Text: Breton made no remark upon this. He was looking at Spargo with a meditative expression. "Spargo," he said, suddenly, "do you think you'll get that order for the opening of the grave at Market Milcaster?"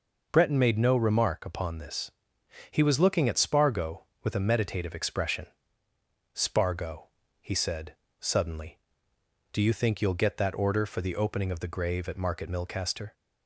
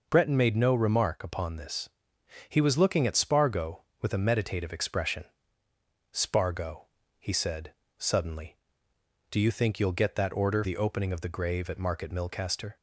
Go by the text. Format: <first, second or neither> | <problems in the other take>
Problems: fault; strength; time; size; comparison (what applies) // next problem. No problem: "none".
first | skips "for"; at 10.6 s